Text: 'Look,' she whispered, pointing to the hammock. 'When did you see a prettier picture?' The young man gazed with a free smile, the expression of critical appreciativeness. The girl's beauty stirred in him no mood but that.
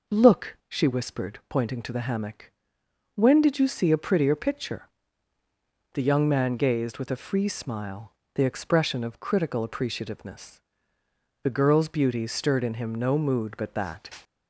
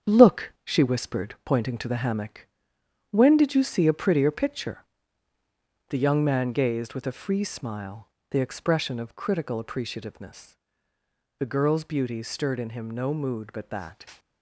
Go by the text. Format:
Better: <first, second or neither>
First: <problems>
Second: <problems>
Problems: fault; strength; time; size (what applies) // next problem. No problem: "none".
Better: first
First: none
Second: gets quieter; strong; throughout; 8.5 dB